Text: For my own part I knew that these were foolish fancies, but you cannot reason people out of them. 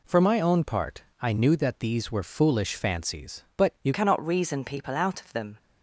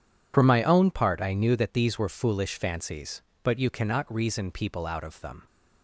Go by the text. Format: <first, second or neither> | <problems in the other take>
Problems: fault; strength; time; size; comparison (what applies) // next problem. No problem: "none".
second | pauses between "part" and "I"; slight; at 1.0 s; 0.18 s long // changes voice at "cannot"; from 3.9 s on; 1.6 s long